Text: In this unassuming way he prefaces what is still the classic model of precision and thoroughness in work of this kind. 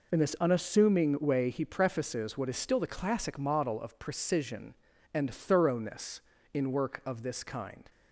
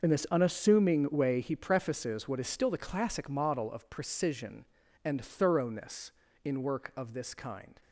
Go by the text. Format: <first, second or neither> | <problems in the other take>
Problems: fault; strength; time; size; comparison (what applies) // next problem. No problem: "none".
first | gets quieter; strong; throughout; 14 dB